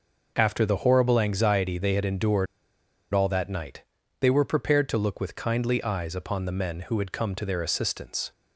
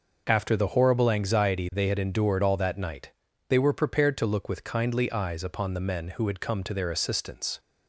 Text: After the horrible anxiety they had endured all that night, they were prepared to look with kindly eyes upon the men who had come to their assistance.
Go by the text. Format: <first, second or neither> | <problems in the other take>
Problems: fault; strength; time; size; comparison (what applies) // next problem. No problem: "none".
second | pauses between "endured" and "all"; noticeable; at 2.4 s; 0.66 s long